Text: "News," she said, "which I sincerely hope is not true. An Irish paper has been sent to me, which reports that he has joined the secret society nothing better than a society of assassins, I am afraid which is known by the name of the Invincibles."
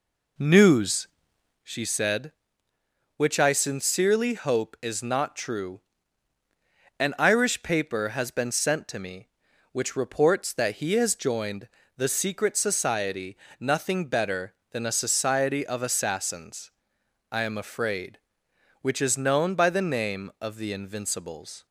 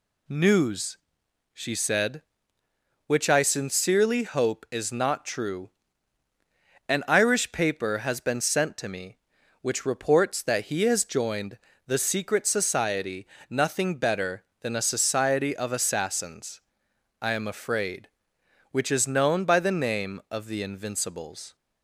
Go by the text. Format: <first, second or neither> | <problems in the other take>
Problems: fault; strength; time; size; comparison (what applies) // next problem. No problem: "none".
second | starts louder than the rest; slight; until 1.7 s; 3.5 dB // pauses between "joined" and "the"; slight; at 11.6 s; 0.26 s long; slight in the second // pauses between "society" and "nothing"; slight; at 13.3 s; 0.22 s long; slight in the second